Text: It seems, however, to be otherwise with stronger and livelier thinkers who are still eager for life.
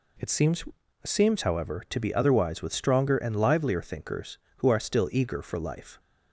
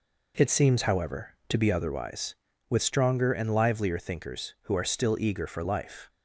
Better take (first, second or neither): second